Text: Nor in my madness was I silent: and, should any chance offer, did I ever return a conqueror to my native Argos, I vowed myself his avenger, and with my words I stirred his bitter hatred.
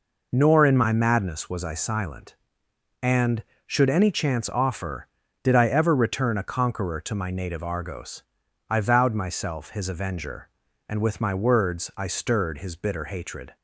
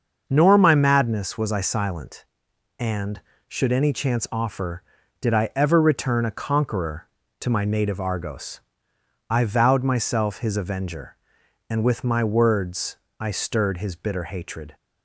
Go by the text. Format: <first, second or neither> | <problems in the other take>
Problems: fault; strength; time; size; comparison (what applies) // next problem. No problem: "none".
first | starts louder than the rest; until 1.2 s; 6.5 dB // skips "in"; at 0.5 s // pauses between "words" and "I"; slight; at 12.9 s; 0.24 s long